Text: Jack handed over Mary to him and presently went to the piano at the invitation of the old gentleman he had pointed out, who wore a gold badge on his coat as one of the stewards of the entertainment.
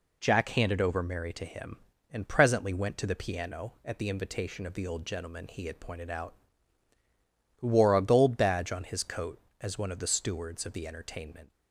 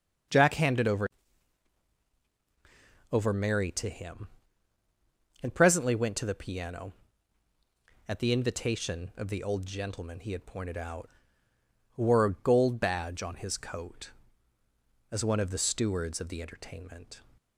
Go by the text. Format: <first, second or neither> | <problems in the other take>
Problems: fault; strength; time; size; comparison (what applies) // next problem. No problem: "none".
first | starts louder than the rest; until 3.3 s; 6.5 dB // says "over" twice; at 3.1 s